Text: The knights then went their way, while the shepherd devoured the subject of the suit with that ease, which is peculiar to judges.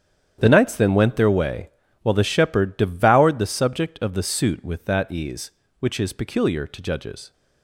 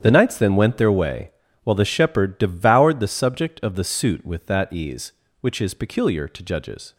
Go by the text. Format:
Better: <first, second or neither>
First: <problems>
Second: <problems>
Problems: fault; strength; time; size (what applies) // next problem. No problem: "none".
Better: neither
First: starts louder than the rest; strong; until 1.4 s; 9.5 dB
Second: starts louder than the rest; strong; until 1.0 s; 9.5 dB